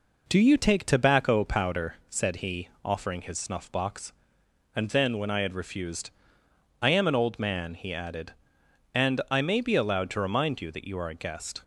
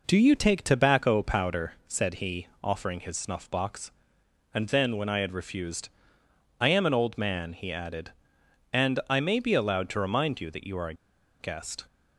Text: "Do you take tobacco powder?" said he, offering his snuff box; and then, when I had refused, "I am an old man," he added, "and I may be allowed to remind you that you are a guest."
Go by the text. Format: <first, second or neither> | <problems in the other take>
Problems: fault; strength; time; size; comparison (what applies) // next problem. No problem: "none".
first | pauses between "a" and "guest"; noticeable; at 10.9 s; 0.46 s long